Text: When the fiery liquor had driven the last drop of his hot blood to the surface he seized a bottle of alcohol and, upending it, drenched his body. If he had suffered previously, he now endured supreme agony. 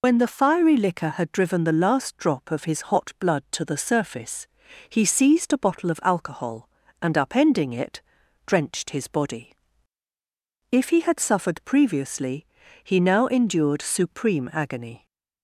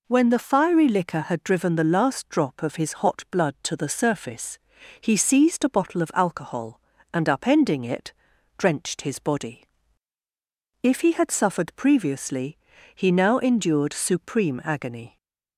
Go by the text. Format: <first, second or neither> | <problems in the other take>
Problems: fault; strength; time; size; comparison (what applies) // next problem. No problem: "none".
second | loses the start of "When"; at 0.0 s; 85 ms // pauses between "surface" and "he"; at 4.4 s; 0.42 s long; also in the second